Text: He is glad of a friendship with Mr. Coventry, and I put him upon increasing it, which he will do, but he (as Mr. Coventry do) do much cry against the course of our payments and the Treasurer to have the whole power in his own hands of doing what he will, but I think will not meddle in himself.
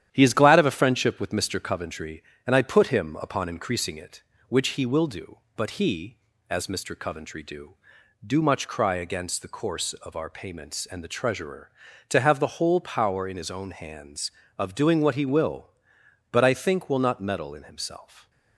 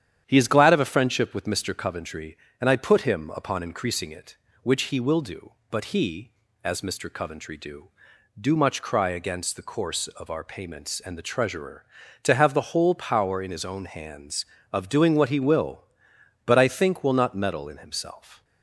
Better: second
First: gets quieter; noticeable; throughout; 4.5 dB // starts louder than the rest; strong; until 1.1 s; 10.5 dB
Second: starts louder than the rest; strong; until 1.2 s; 9.5 dB

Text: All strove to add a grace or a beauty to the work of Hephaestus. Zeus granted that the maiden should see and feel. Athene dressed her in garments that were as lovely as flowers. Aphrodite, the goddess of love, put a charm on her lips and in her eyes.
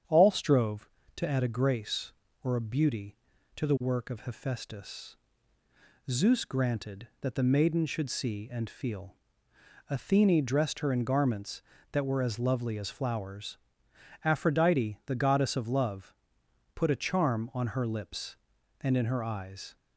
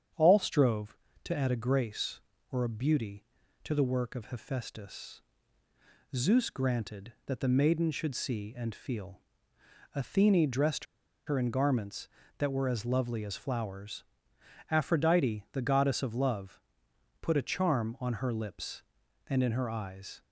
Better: first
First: starts louder than the rest; strong; until 1.3 s; 8.5 dB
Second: starts louder than the rest; strong; until 1.4 s; 8.5 dB // pauses between "dressed" and "her"; at 10.8 s; 0.41 s long

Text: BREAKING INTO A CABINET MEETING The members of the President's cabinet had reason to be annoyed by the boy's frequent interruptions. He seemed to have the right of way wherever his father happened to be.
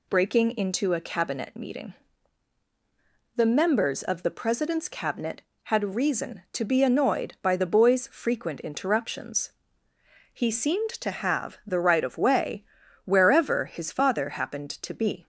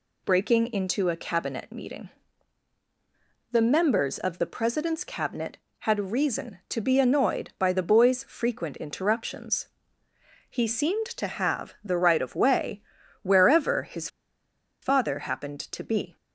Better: first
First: pauses between "MEETING" and "The"; strong; at 1.9 s; 1.4 s long // pauses between "way" and "wherever"; at 12.6 s; 0.40 s long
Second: pauses between "MEETING" and "The"; strong; at 2.0 s; 1.4 s long // pauses between "way" and "wherever"; at 12.8 s; 0.40 s long // pauses between "his" and "father"; noticeable; at 14.0 s; 0.74 s long

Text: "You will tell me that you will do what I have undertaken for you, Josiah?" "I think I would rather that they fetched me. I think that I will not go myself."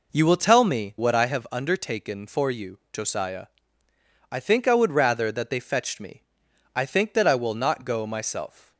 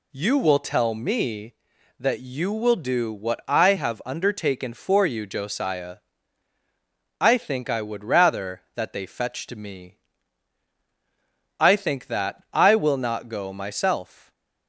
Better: second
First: skips "that you will do"; at 0.9 s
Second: none

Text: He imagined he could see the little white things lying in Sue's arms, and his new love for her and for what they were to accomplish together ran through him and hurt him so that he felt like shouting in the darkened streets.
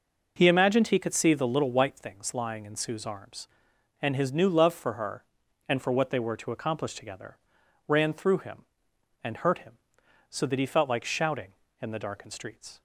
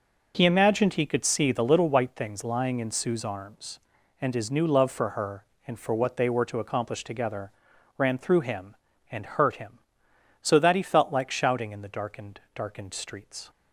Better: first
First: pauses between "together" and "ran"; noticeable; at 7.3 s; 0.48 s long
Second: pauses between "together" and "ran"; at 7.5 s; 0.44 s long // says "darkened" twice; at 12.5 s

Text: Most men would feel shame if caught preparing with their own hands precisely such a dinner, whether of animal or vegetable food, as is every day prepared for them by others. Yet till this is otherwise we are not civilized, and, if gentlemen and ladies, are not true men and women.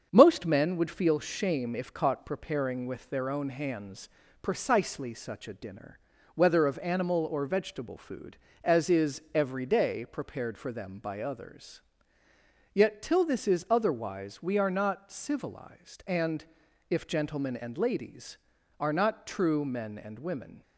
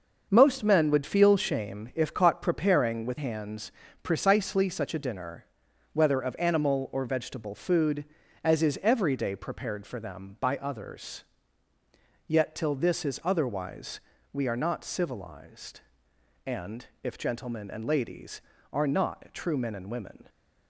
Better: first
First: starts louder than the rest; strong; until 1.1 s; 7 dB // pauses between "hands" and "precisely"; slight; at 4.0 s; 0.32 s long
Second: starts louder than the rest; until 1.3 s; 6.5 dB // skips "their own"; at 3.1 s // pauses between "hands" and "precisely"; slight; at 3.7 s; 0.32 s long // pauses between "otherwise" and "we"; slight; at 13.9 s; 0.34 s long

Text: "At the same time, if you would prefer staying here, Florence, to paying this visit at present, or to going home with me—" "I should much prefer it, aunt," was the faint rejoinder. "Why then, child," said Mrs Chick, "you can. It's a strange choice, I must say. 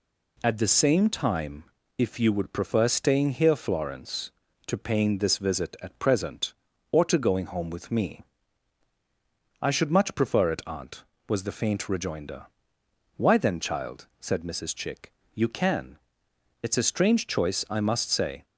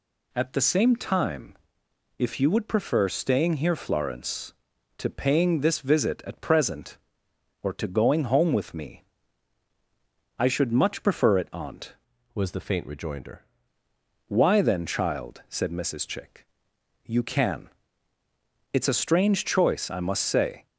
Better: first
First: none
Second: changes voice from "was" to "rejoinder"; from 12.3 to 13.4 s; 1.1 s long

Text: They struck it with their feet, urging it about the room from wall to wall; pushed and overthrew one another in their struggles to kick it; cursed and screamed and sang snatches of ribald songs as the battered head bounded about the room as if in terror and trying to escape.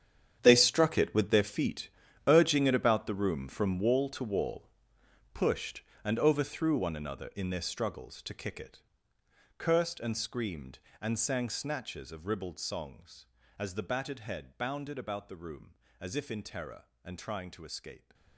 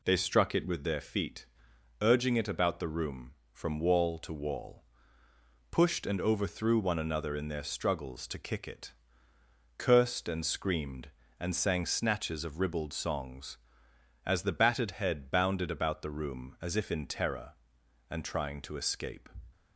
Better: second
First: gets quieter; strong; throughout; 15 dB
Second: none

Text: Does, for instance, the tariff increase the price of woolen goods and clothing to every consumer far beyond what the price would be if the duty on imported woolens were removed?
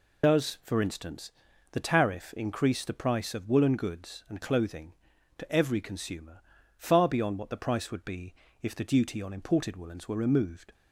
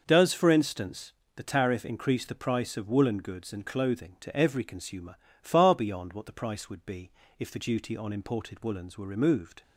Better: second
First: loses the start of "Does"; at 0.2 s; 85 ms // pauses between "consumer" and "far"; slight; at 6.4 s; 0.36 s long // pauses between "be" and "if"; slight; at 8.3 s; 0.28 s long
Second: pauses between "consumer" and "far"; slight; at 5.1 s; 0.24 s long // pauses between "be" and "if"; slight; at 7.0 s; 0.28 s long

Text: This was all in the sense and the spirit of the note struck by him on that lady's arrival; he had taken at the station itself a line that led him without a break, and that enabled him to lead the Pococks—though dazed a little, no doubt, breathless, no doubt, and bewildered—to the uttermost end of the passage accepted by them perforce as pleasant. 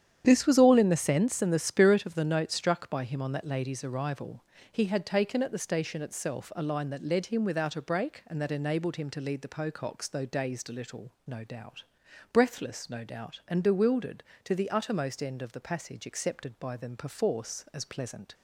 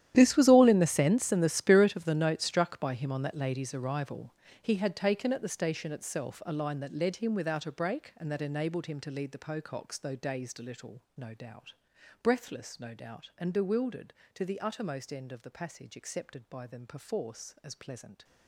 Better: first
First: starts louder than the rest; strong; until 1.2 s; 9.5 dB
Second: gets quieter; strong; throughout; 18 dB // starts louder than the rest; strong; until 1.1 s; 11.5 dB

